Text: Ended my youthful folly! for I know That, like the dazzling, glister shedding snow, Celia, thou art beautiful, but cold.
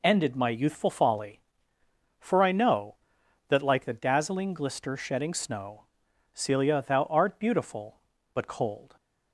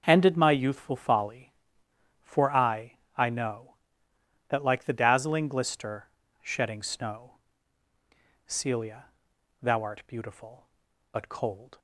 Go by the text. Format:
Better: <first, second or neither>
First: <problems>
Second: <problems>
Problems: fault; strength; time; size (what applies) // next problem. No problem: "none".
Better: first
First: none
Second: starts louder than the rest; noticeable; until 1.0 s; 6 dB // says "I" twice; at 3.1 s // pauses between "glister" and "shedding"; slight; at 6.0 s; 0.34 s long